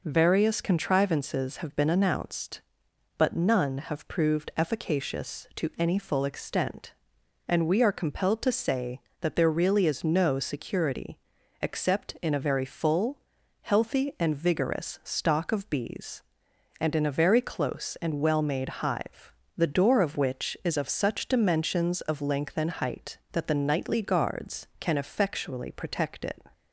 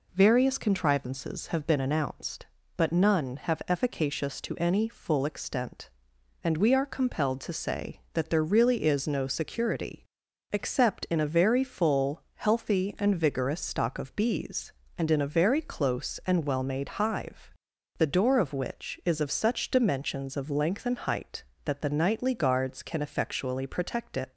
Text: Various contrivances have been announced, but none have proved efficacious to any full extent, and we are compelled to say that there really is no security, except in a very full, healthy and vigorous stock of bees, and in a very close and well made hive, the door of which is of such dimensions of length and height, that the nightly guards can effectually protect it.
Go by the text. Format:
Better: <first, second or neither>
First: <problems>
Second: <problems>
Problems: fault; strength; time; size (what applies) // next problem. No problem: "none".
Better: first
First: none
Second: skips "proved"; at 3.6 s